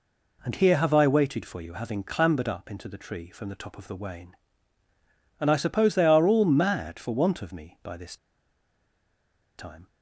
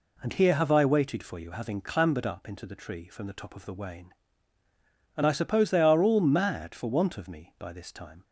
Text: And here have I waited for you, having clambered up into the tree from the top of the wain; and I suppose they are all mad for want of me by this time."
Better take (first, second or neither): second